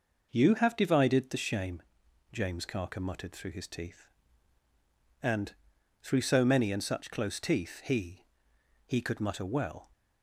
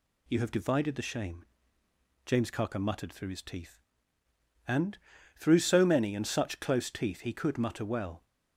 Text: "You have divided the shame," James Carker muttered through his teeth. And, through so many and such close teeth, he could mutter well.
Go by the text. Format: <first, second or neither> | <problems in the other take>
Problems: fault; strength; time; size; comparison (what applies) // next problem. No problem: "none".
second | says "he" twice; at 8.8 s